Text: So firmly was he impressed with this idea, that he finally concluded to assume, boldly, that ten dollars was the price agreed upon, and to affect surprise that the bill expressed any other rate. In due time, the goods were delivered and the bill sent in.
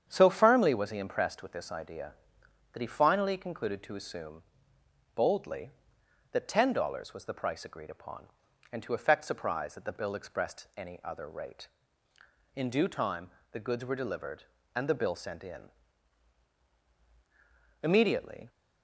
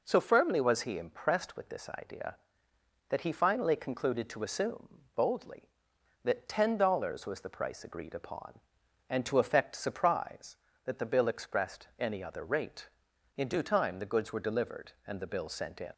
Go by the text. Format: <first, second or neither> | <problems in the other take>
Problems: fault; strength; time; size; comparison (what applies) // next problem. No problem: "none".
second | starts louder than the rest; strong; until 1.0 s; 8 dB // goes on to say "Immediately"; noticeable; from 17.8 s on; 0.66 s long